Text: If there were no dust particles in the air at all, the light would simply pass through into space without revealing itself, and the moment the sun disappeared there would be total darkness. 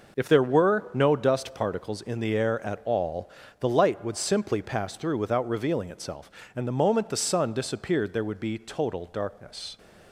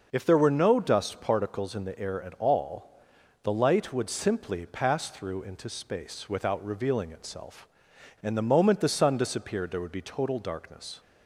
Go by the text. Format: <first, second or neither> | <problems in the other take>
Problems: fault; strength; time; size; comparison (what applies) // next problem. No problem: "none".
second | skips "into space"; at 5.1 s